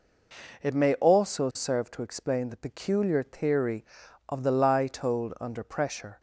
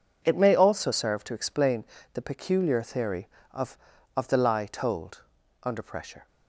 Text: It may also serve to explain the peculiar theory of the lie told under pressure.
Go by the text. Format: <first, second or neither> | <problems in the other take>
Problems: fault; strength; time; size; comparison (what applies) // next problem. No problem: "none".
first | pauses between "explain" and "the"; slight; at 1.8 s; 0.28 s long // says "of" twice; at 4.1 s // pauses between "told" and "under"; at 5.2 s; 0.40 s long